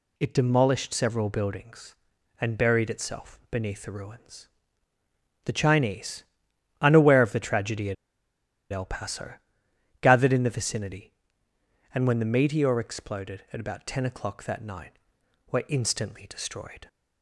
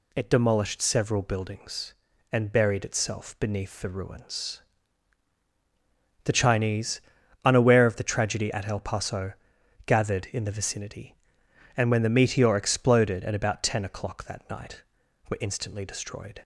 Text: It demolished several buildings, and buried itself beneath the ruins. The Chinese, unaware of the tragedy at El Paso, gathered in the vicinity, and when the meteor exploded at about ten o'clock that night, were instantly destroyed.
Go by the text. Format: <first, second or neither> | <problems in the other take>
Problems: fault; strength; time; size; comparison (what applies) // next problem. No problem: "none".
second | pauses between "at" and "El"; noticeable; at 7.9 s; 0.78 s long